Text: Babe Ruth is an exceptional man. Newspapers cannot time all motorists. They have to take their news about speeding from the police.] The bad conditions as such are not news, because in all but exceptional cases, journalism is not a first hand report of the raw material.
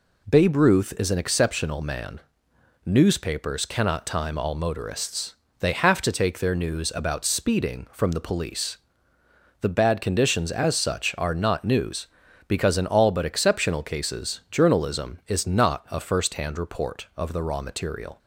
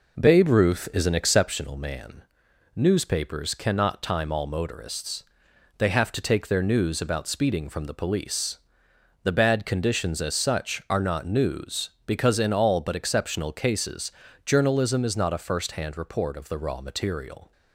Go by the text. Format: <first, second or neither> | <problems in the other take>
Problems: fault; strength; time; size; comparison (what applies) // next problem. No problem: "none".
first | starts louder than the rest; noticeable; until 1.5 s; 4.5 dB